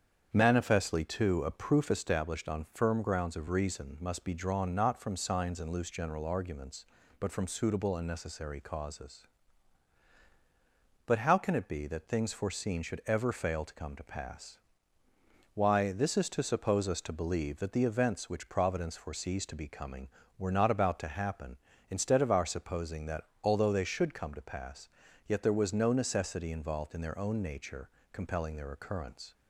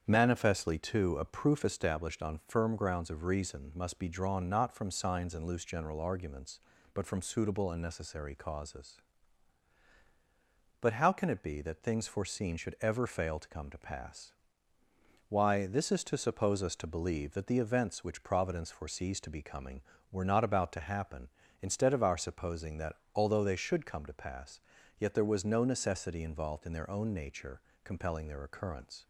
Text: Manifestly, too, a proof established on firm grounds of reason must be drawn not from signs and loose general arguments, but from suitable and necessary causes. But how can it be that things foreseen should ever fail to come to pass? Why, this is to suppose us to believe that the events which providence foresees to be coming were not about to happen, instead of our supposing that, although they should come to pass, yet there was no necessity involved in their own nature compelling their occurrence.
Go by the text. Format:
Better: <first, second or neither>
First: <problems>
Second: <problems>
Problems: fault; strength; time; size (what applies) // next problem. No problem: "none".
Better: neither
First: starts louder than the rest; strong; until 1.3 s; 8 dB // pauses between "nature" and "compelling"; slight; at 27.8 s; 0.24 s long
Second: starts louder than the rest; strong; until 1.0 s; 8 dB // pauses between "nature" and "compelling"; slight; at 27.6 s; 0.24 s long